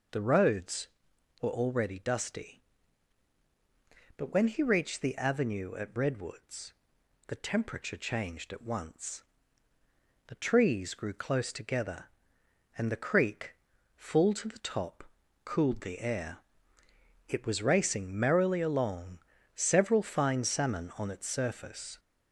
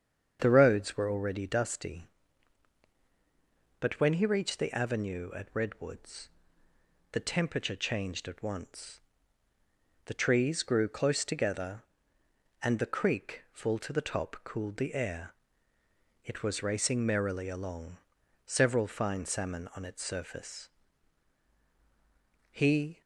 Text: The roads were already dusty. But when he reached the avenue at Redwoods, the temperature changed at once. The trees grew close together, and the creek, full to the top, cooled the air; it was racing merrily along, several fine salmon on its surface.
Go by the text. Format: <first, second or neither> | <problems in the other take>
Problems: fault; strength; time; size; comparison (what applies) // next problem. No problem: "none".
first | starts louder than the rest; strong; until 1.4 s; 7.5 dB // goes on to say "He"; from 22.5 s on; 0.50 s long